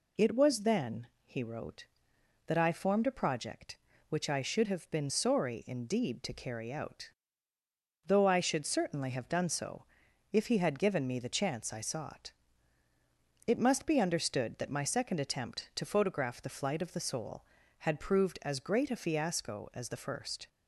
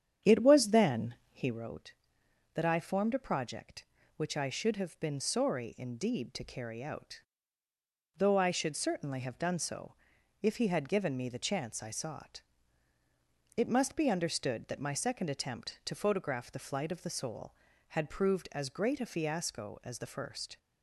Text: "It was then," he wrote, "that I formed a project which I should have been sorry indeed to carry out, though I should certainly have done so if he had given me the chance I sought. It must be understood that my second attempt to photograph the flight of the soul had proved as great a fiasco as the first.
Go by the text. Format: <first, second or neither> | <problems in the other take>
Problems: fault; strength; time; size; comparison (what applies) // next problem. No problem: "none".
first | starts louder than the rest; strong; until 1.7 s; 8.5 dB // pauses between "so" and "if"; noticeable; at 9.9 s; 0.48 s long; noticeable in the first